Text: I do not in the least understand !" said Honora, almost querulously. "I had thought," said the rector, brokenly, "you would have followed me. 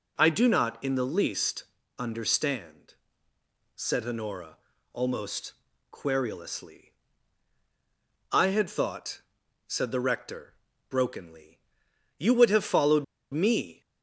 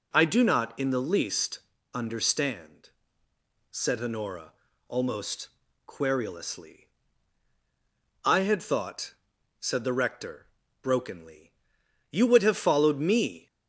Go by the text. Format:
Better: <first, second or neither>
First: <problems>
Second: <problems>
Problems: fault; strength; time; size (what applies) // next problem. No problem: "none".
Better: second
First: pauses between "least" and "understand"; slight; at 1.6 s; 0.34 s long // pauses between "almost" and "querulously"; at 5.5 s; 0.38 s long // pauses between "followed" and "me"; slight; at 13.0 s; 0.27 s long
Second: pauses between "least" and "understand"; slight; at 1.5 s; 0.34 s long // pauses between "almost" and "querulously"; at 5.4 s; 0.38 s long